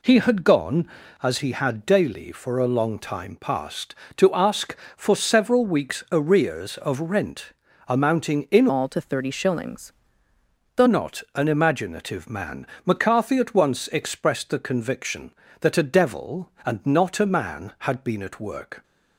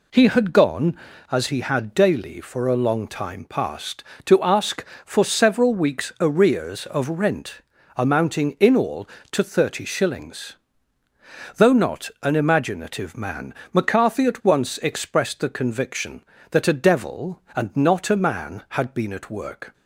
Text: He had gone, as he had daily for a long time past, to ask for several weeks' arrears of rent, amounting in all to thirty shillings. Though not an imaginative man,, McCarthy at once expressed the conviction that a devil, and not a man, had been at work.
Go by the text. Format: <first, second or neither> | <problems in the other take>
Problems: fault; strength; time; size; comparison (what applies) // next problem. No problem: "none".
second | changes voice from "all" to "Though"; from 8.6 to 10.8 s; 2.2 s long